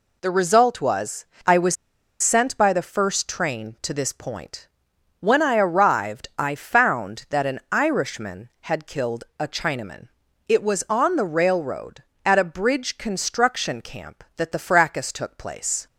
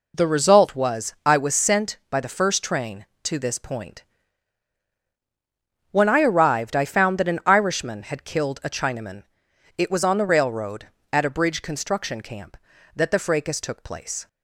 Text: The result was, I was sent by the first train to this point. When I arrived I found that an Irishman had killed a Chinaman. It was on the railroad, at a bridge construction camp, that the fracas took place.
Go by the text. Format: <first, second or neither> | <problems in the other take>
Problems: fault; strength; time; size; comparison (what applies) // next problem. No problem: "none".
second | pauses between "was" and "sent"; at 1.7 s; 0.44 s long